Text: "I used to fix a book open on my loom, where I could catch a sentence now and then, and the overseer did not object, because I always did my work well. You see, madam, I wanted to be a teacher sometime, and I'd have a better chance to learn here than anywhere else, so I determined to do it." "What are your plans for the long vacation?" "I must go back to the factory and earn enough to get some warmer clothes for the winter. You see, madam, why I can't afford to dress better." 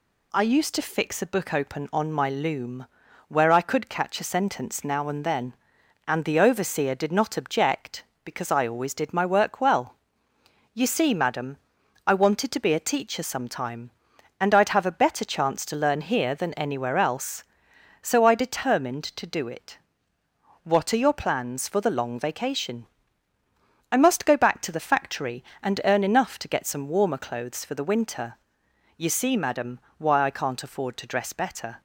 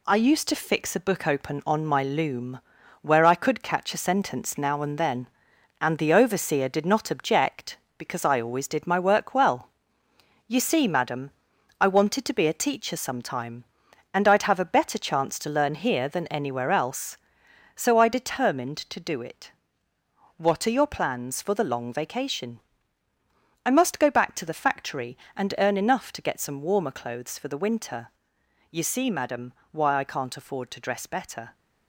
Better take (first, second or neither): first